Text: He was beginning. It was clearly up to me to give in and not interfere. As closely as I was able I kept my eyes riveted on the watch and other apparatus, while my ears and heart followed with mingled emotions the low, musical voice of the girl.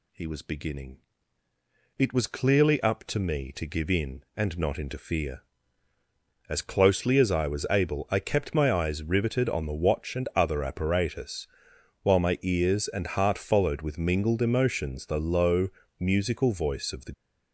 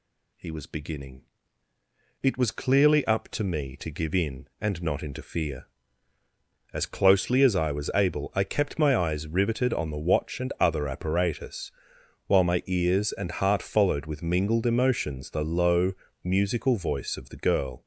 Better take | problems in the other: second | stops before "girl"; at 17.1 s

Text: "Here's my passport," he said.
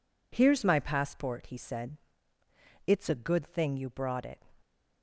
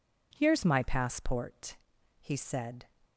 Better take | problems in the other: second | goes on to say "It's a good thing you brought it"; from 2.8 s on; 1.5 s long

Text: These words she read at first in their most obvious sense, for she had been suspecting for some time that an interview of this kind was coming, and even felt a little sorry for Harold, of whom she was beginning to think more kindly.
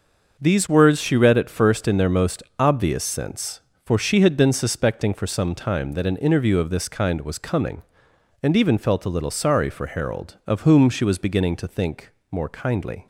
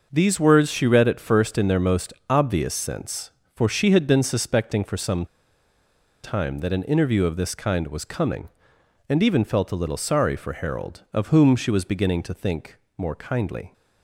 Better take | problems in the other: first | starts louder than the rest; noticeable; until 1.1 s; 6 dB; also in the first // pauses between "most" and "obvious"; slight; at 2.1 s; 0.16 s long; slight in the first // pauses between "some" and "time"; at 5.2 s; 0.98 s long // pauses between "think" and "more"; slight; at 12.7 s; 0.20 s long; slight in the first

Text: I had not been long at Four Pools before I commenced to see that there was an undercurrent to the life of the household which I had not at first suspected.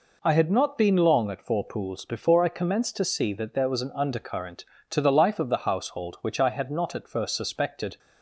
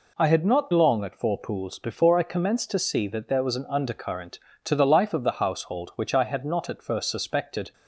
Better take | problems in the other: first | skips "been"; at 0.7 s

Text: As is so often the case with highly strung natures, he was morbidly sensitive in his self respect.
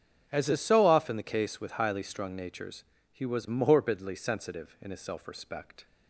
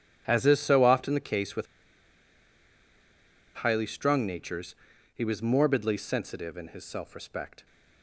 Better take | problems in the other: first | starts louder than the rest; strong; until 1.2 s; 9 dB; strong in the first // pauses between "with" and "highly"; strong; at 1.6 s; 1.9 s long

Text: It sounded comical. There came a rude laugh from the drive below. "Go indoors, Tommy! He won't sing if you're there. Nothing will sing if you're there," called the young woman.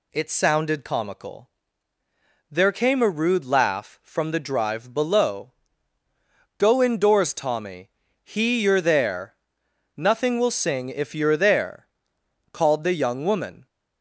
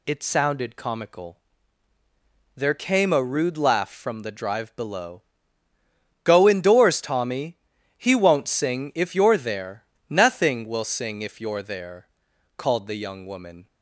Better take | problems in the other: second | skips "won't sing if"; at 8.6 s

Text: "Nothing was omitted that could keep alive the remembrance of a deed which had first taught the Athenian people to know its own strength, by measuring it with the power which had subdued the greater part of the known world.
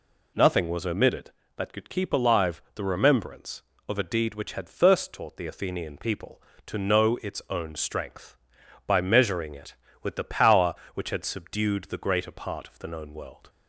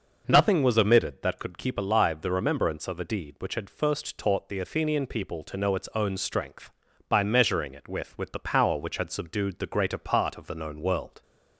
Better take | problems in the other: first | says "with" twice; at 8.1 s

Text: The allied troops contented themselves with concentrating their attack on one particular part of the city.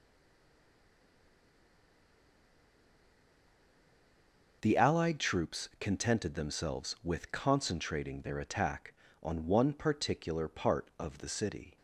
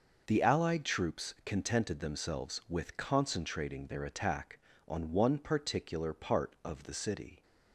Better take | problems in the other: second | stays silent before the first word; strong; until 4.6 s; 4.6 s long

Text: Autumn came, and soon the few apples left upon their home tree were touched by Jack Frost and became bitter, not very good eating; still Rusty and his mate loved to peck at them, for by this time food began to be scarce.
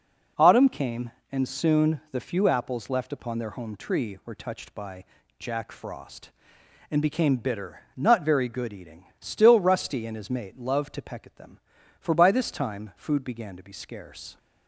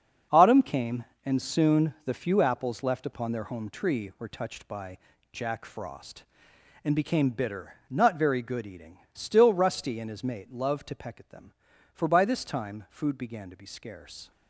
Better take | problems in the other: first | gets quieter; strong; throughout; 10.5 dB // pauses between "by" and "Jack"; slight; at 4.9 s; 0.34 s long; slight in the first

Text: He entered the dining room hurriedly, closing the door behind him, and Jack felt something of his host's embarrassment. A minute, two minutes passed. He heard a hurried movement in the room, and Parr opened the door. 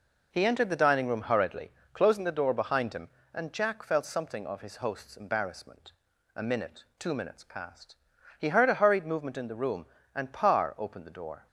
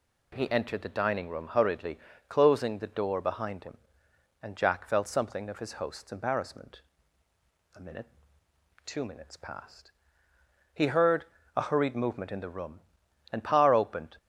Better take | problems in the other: first | pauses between "heard" and "a"; slight; at 11.2 s; 0.30 s long // stops before "the door"; at 14.1 s

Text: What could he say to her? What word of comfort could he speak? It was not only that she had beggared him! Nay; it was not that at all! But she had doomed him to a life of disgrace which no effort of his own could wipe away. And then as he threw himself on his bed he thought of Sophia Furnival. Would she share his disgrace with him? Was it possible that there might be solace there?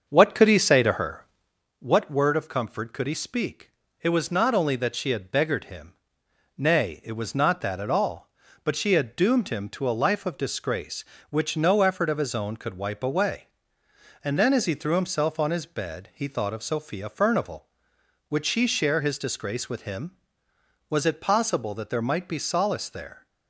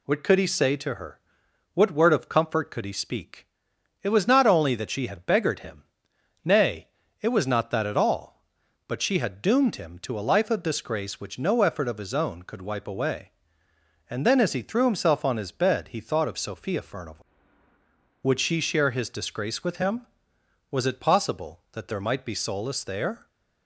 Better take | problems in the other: second | starts louder than the rest; until 1.6 s; 6.5 dB

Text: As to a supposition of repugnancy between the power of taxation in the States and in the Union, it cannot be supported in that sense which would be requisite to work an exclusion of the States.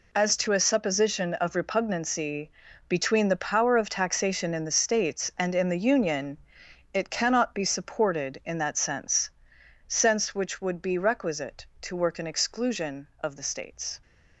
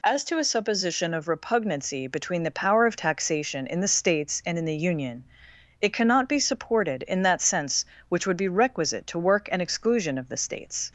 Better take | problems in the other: second | pauses between "repugnancy" and "between"; at 2.5 s; 0.38 s long // says "sense" twice; at 9.8 s

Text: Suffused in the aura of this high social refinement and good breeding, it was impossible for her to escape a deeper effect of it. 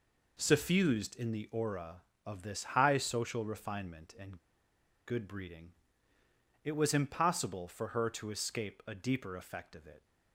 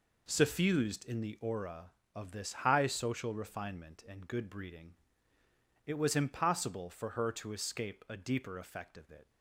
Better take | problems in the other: second | pauses between "and" and "good"; noticeable; at 4.3 s; 0.69 s long

